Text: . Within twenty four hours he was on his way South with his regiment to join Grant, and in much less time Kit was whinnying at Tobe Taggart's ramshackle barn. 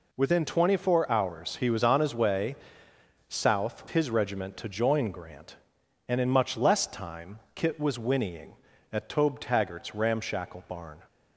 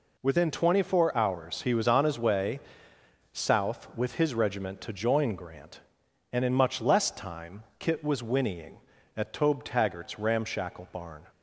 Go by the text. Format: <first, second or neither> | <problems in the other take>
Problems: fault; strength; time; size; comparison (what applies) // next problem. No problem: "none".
second | pauses between "way" and "South"; noticeable; at 2.5 s; 0.74 s long; noticeable in the second // skips "with"; at 3.8 s